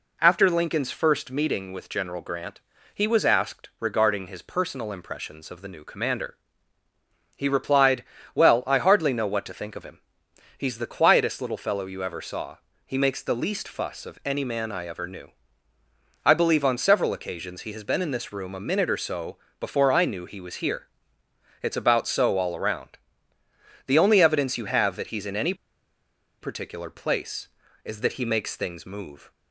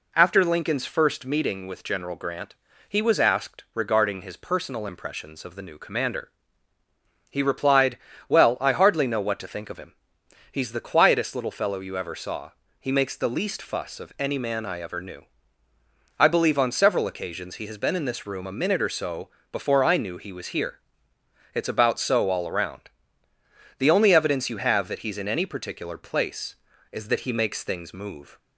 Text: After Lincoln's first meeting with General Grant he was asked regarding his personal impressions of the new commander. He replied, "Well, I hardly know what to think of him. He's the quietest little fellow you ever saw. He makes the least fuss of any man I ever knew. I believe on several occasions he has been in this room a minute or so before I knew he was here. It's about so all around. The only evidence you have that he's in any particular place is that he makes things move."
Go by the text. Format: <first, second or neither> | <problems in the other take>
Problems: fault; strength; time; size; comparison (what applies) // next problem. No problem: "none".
second | pauses between "Grant" and "he"; slight; at 2.5 s; 0.36 s long; slight in the second // pauses between "so" and "before"; slight; at 19.3 s; 0.20 s long; slight in the second // pauses between "any" and "particular"; noticeable; at 25.5 s; 0.87 s long